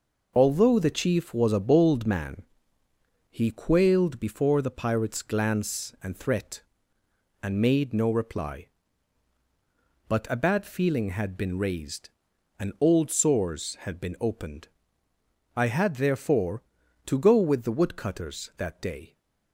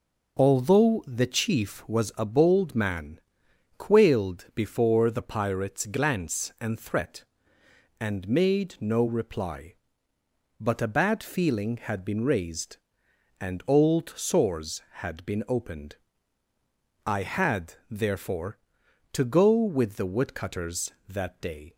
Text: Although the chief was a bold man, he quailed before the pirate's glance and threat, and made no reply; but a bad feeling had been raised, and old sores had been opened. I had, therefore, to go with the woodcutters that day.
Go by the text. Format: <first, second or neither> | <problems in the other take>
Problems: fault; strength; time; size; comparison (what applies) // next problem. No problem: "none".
first | skips "he"; at 3.4 s